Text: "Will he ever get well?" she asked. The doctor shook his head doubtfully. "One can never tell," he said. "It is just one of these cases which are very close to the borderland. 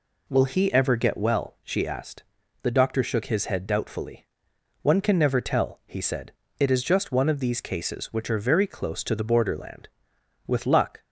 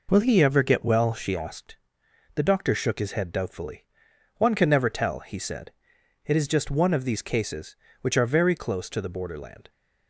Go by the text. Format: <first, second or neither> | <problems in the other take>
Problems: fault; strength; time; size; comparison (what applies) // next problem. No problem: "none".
second | goes on to say "With luck"; from 10.4 s on; 0.56 s long